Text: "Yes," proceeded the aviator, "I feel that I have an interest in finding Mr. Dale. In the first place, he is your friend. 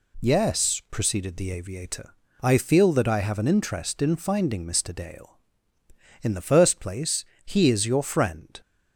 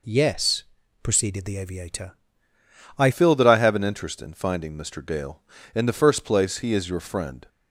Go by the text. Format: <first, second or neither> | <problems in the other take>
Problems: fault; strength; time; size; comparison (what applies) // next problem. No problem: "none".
first | changes voice at "feel"; from 3.1 s on; 4.3 s long